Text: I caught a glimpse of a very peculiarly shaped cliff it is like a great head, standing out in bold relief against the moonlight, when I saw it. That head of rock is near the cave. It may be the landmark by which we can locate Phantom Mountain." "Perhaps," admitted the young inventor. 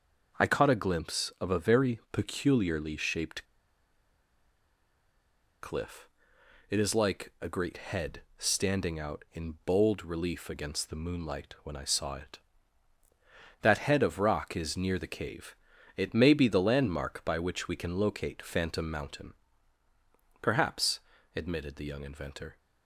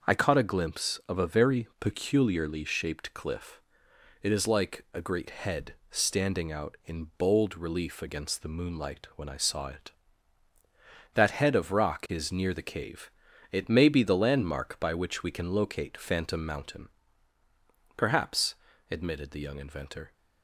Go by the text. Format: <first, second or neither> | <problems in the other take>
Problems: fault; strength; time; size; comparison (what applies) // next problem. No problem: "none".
second | starts louder than the rest; until 1.4 s; 6.5 dB; also in the second // pauses between "shaped" and "cliff"; strong; at 3.4 s; 2.1 s long // pauses between "cliff" and "it"; noticeable; at 6.0 s; 0.62 s long; noticeable in the second